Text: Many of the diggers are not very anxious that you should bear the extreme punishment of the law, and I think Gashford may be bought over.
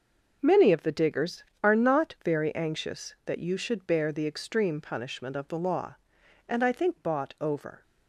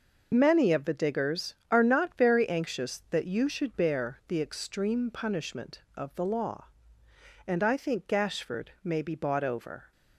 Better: second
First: skips "Gashford may be"; at 6.9 s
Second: none

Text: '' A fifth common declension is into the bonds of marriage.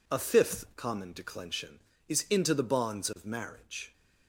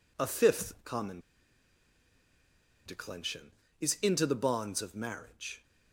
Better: first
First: none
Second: pauses between "common" and "declension"; strong; at 1.2 s; 1.6 s long

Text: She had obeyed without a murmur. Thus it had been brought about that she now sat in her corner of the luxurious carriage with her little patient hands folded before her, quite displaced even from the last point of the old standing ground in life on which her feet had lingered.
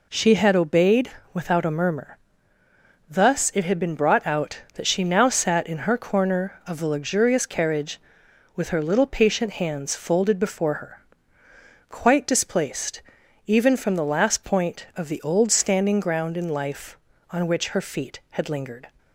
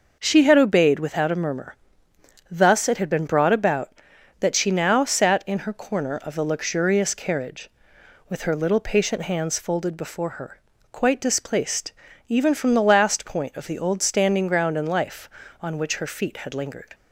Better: second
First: pauses between "obeyed" and "without"; slight; at 1.1 s; 0.24 s long // says "out" for "about"; at 4.2 s // pauses between "displaced" and "even"; at 13.0 s; 0.44 s long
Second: pauses between "displaced" and "even"; slight; at 11.9 s; 0.34 s long

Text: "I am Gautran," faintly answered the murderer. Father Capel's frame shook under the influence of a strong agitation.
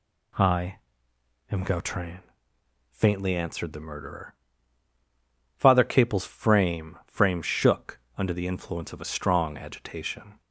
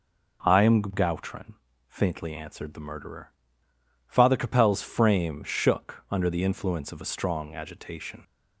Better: second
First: pauses between "I" and "am"; noticeable; at 0.7 s; 0.74 s long // says "frame" twice; at 7.0 s // pauses between "shook" and "under"; slight; at 7.9 s; 0.18 s long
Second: none

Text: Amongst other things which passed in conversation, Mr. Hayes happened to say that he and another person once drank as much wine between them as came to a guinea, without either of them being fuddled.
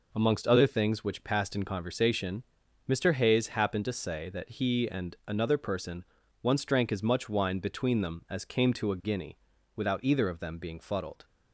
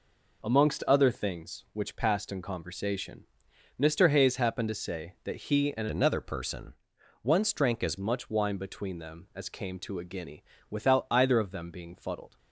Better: first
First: pauses between "person" and "once"; at 6.0 s; 0.38 s long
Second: changes voice from "another" to "as"; from 5.9 to 7.9 s; 2.0 s long // pauses between "person" and "once"; noticeable; at 6.7 s; 0.48 s long

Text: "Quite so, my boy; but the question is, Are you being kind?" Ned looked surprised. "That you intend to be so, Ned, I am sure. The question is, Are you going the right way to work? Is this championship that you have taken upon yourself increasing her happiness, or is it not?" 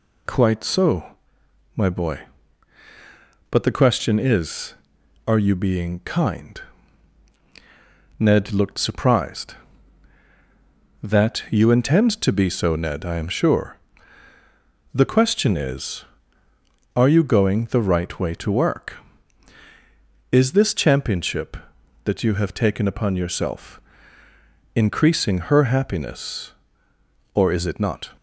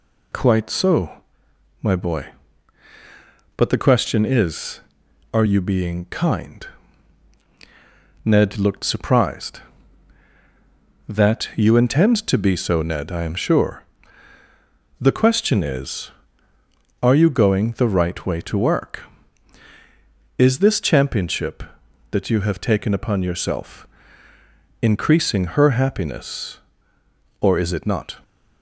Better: neither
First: pauses between "yourself" and "increasing"; noticeable; at 23.7 s; 0.94 s long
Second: pauses between "yourself" and "increasing"; noticeable; at 23.8 s; 0.94 s long

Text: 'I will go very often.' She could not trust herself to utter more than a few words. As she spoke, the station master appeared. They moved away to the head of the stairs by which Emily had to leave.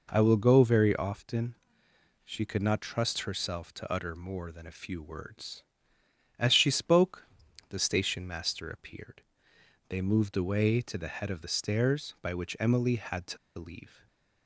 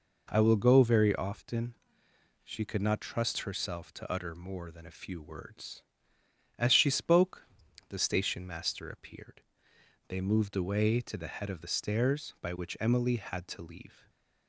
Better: second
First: pauses between "to" and "leave"; slight; at 13.3 s; 0.20 s long // stays silent after the last word; slight; from 13.8 s on; 0.6 s long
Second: stays silent after the last word; slight; from 13.8 s on; 0.6 s long

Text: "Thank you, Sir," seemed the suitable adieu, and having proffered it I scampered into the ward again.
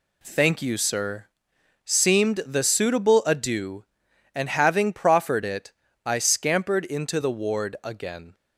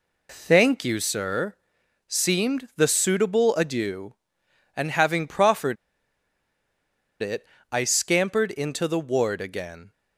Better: first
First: pauses between "it" and "I"; slight; at 5.7 s; 0.34 s long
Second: pauses between "proffered" and "it"; strong; at 5.7 s; 1.4 s long // pauses between "it" and "I"; slight; at 7.4 s; 0.24 s long

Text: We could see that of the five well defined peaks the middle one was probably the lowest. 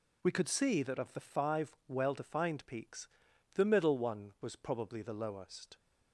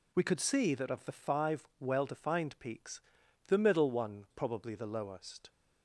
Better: first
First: pauses between "peaks" and "the"; noticeable; at 3.0 s; 0.46 s long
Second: pauses between "peaks" and "the"; noticeable; at 3.0 s; 0.46 s long // skips "was"; at 4.2 s

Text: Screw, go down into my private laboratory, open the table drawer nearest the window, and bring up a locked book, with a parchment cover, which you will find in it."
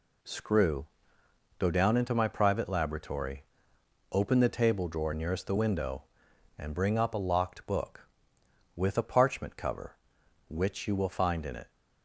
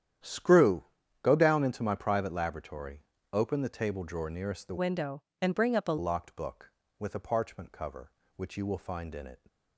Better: first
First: none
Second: starts louder than the rest; strong; until 1.6 s; 10 dB // changes voice from "window" to "a"; from 4.7 to 5.9 s; 1.2 s long

